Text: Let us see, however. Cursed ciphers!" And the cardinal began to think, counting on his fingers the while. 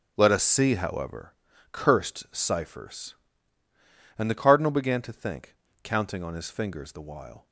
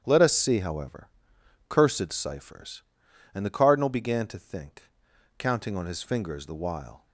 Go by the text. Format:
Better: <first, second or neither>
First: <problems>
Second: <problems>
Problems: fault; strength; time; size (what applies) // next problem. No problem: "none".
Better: neither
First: starts louder than the rest; strong; until 1.1 s; 8.5 dB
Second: starts louder than the rest; strong; until 1.0 s; 9.5 dB